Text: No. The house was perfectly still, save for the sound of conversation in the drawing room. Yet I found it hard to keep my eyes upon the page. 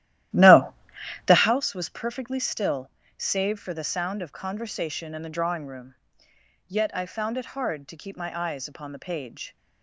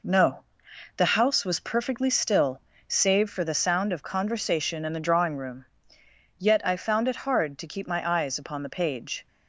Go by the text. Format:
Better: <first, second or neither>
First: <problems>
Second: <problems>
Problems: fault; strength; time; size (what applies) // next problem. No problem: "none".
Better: second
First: starts louder than the rest; strong; until 1.6 s; 13.5 dB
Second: none